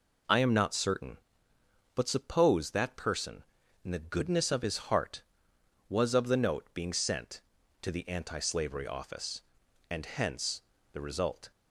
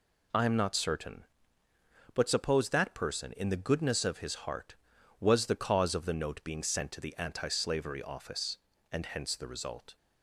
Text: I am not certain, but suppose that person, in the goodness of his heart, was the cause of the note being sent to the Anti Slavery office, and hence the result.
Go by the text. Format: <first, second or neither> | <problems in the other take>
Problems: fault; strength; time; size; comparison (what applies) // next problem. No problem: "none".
second | skips "the cause"; at 6.1 s // pauses between "hence" and "the"; slight; at 10.6 s; 0.30 s long